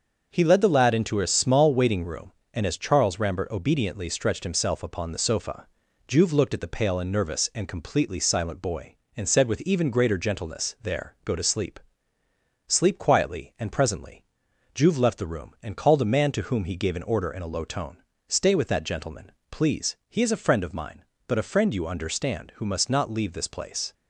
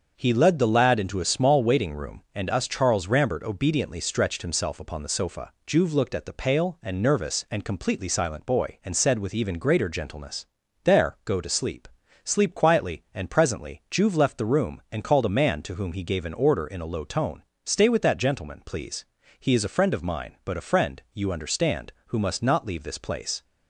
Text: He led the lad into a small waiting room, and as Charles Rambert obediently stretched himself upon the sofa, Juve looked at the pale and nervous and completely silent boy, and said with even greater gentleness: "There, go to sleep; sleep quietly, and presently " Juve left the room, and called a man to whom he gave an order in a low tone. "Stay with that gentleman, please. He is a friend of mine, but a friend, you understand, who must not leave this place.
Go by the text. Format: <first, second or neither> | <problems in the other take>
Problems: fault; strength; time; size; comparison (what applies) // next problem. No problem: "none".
first | starts louder than the rest; until 1.1 s; 6.5 dB; also in the first // says "us" for "as"; at 2.4 s